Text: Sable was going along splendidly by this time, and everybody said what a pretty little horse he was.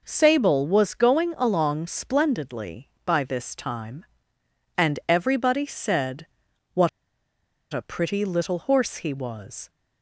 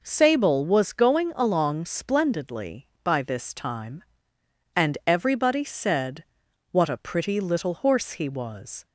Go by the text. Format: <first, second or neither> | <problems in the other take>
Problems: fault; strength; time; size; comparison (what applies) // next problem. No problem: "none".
second | pauses between "said" and "what"; noticeable; at 6.2 s; 0.46 s long; noticeable in the second // pauses between "what" and "a"; noticeable; at 6.8 s; 0.82 s long